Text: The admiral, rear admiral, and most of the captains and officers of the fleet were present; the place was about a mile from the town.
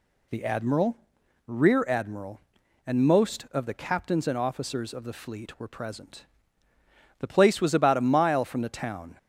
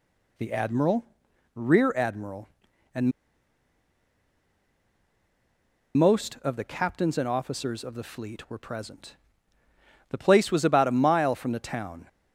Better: first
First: none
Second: pauses between "and" and "most"; strong; at 3.1 s; 2.8 s long

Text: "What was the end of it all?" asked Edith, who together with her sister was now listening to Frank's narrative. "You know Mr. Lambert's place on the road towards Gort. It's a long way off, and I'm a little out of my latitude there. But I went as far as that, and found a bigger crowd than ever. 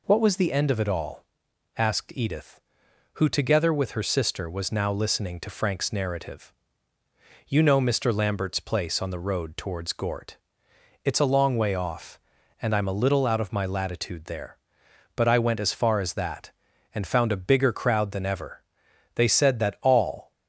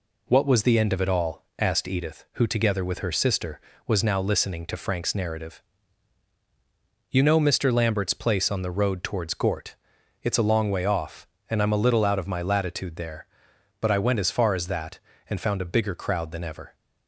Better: second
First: goes on to say "They said that all"; noticeable; from 19.1 s on; 1.1 s long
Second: none

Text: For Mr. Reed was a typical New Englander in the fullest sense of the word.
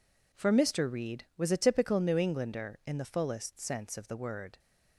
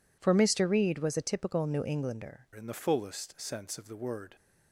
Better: first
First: none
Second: changes voice at "in"; from 2.5 s on; 1.8 s long

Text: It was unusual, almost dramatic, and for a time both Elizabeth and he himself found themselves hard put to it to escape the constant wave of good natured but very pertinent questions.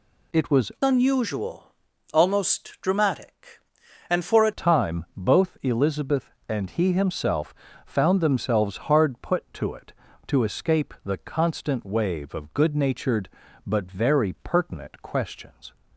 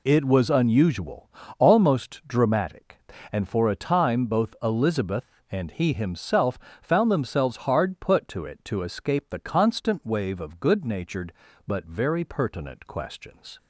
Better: second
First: changes voice from "unusual" to "a"; from 0.8 to 4.5 s; 3.7 s long // pauses between "himself" and "found"; slight; at 7.5 s; 0.32 s long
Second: pauses between "himself" and "found"; slight; at 6.5 s; 0.24 s long

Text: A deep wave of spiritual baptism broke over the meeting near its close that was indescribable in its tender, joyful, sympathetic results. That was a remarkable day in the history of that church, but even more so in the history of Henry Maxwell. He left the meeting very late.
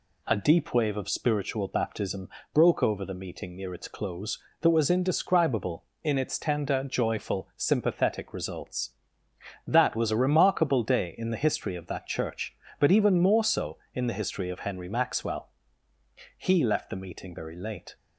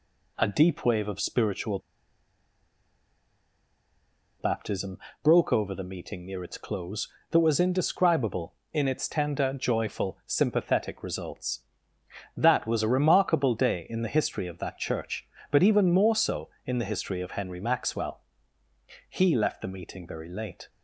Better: first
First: pauses between "baptism" and "broke"; slight; at 2.2 s; 0.24 s long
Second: pauses between "spiritual" and "baptism"; strong; at 1.7 s; 2.6 s long // pauses between "baptism" and "broke"; slight; at 4.9 s; 0.24 s long

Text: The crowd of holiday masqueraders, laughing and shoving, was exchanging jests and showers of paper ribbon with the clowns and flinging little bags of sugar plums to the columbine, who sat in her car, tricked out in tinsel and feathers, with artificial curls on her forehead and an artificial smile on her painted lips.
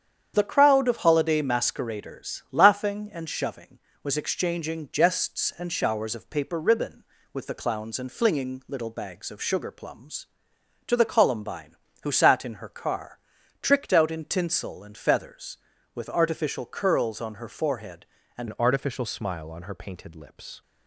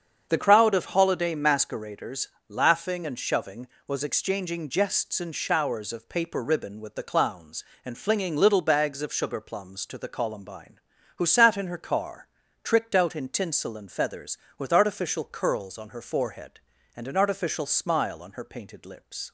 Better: second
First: starts louder than the rest; strong; until 1.3 s; 8.5 dB // changes voice at "an"; from 18.4 s on; 2.2 s long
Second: starts louder than the rest; strong; until 1.3 s; 7 dB

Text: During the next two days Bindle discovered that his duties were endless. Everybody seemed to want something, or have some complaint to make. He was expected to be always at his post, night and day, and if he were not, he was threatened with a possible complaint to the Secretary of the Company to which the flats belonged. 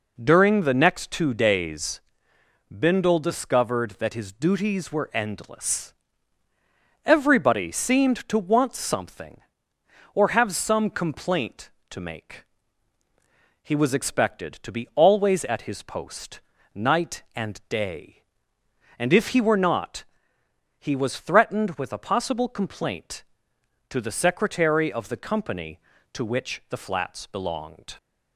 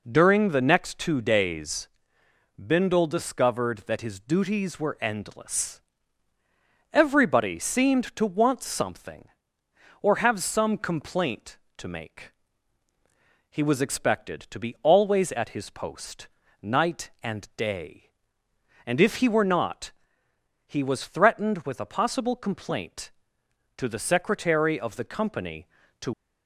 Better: first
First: pauses between "days" and "Bindle"; noticeable; at 1.9 s; 0.72 s long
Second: pauses between "days" and "Bindle"; noticeable; at 1.8 s; 0.72 s long // stops before "which the flats belonged"; at 26.1 s

